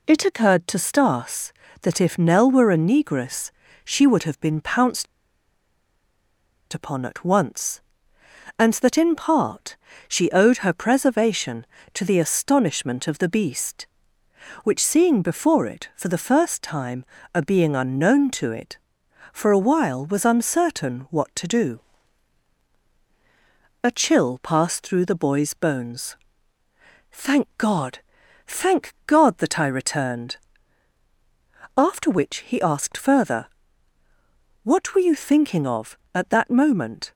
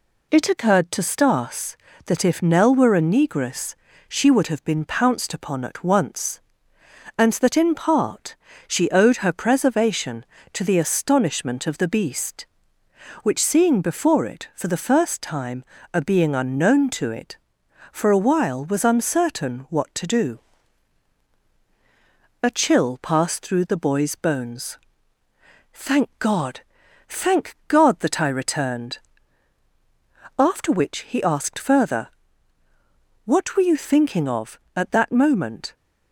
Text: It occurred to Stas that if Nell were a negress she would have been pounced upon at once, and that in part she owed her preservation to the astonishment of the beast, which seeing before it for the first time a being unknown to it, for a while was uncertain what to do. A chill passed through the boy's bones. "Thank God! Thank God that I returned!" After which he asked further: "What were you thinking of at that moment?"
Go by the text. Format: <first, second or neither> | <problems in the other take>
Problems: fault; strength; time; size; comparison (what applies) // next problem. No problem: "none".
second | pauses between "negress" and "she"; slight; at 3.5 s; 0.32 s long; slight in the second // pauses between "pounced" and "upon"; strong; at 5.0 s; 1.6 s long // pauses between "part" and "she"; slight; at 9.7 s; 0.32 s long; slight in the second // pauses between "time" and "a"; slight; at 17.0 s; 0.32 s long; slight in the second